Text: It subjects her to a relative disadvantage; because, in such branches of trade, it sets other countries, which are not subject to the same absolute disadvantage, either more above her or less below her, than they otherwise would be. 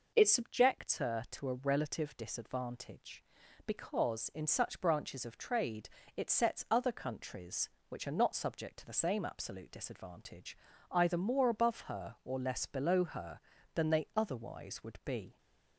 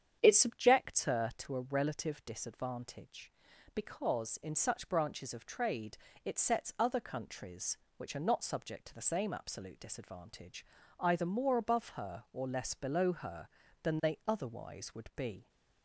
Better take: first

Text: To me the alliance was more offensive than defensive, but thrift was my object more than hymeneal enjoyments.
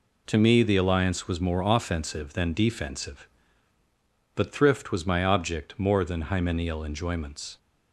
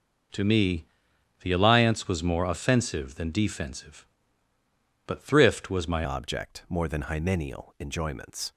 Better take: first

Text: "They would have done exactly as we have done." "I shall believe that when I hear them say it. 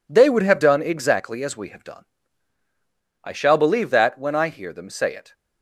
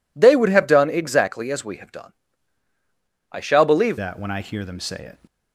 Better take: first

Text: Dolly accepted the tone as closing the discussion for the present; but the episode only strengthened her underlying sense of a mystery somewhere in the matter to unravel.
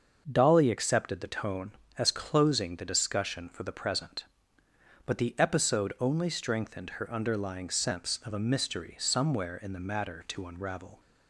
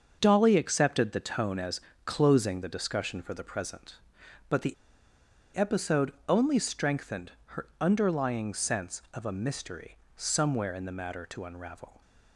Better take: first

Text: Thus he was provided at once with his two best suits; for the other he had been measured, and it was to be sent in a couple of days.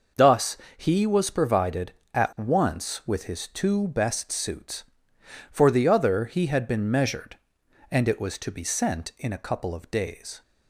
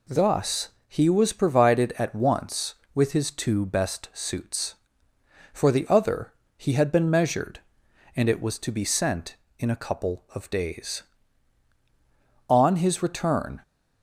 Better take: first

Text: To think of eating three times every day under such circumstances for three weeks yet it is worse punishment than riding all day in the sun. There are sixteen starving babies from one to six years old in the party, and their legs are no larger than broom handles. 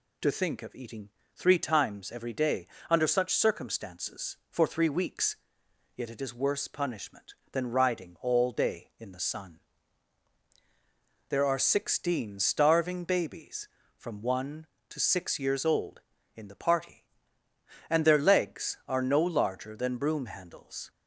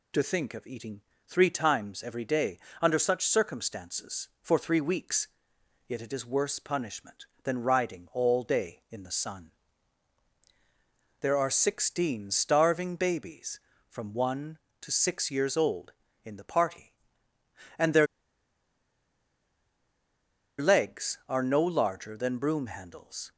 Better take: first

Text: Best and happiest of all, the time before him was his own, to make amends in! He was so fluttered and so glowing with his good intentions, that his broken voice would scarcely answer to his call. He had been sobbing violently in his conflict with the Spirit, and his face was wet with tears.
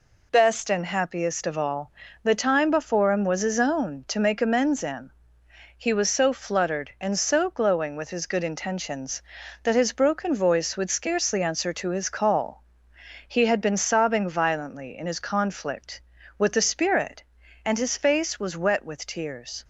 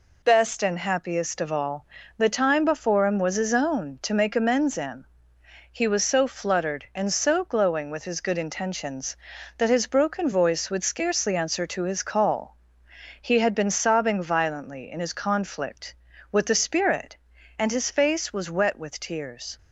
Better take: neither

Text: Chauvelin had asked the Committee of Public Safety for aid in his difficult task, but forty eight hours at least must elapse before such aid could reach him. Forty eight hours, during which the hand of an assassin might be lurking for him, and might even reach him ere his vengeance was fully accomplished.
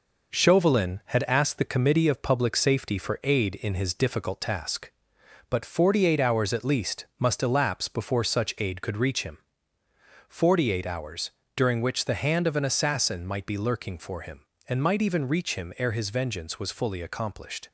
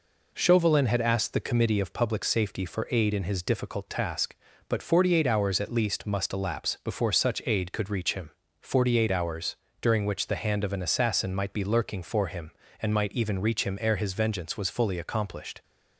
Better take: second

